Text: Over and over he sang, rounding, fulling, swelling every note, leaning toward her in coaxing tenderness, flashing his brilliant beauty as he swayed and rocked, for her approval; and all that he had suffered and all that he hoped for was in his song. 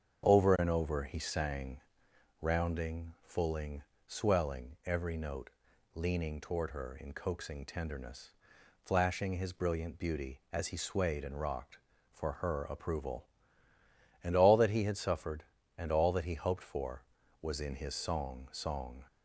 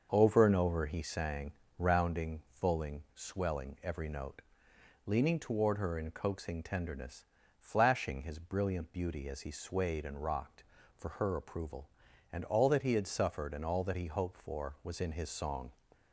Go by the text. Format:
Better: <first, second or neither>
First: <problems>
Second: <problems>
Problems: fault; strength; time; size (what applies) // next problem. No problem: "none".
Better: second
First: starts louder than the rest; strong; until 1.3 s; 7 dB // says "song" twice; at 18.5 s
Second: starts louder than the rest; until 1.1 s; 6 dB